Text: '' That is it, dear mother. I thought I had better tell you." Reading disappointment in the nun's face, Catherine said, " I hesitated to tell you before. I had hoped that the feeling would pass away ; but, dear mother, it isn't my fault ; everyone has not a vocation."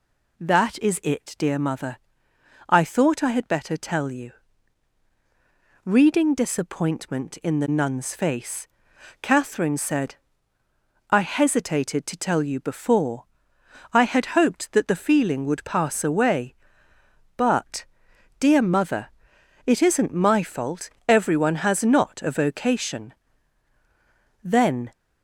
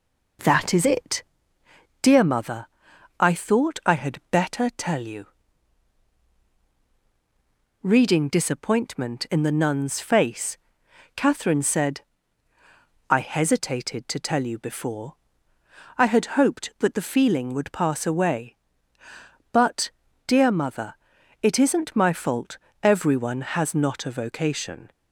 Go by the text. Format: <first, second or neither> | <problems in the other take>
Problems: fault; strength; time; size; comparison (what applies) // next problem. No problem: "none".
second | goes on to say "Then"; slight; from 24.4 s on; 0.48 s long